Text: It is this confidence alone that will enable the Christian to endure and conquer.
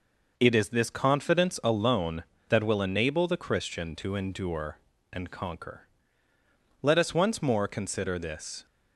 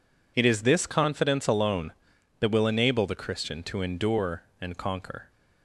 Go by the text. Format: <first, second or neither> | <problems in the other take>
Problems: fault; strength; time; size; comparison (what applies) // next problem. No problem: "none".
second | goes on to say "Let us once more consider this"; strong; from 6.8 s on; 1.8 s long